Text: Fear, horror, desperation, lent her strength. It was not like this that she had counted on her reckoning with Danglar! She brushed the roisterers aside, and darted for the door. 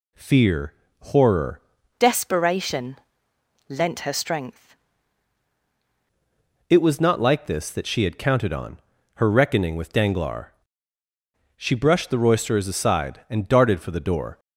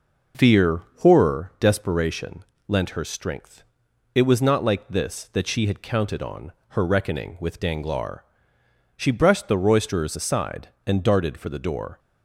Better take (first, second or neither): second